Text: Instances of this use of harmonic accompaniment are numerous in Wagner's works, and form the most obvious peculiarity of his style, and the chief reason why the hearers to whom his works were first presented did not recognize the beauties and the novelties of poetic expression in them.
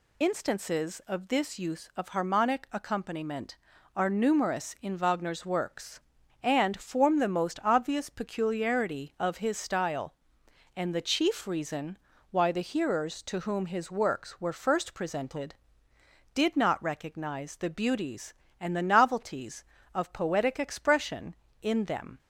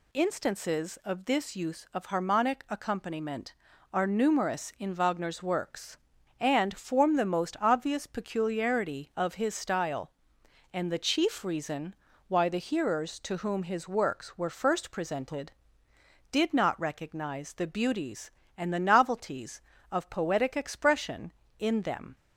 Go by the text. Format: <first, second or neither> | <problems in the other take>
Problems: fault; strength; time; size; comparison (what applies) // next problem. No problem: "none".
second | loses the start of "Instances"; at 0.2 s; 45 ms // pauses between "reason" and "why"; slight; at 11.9 s; 0.34 s long; slight in the second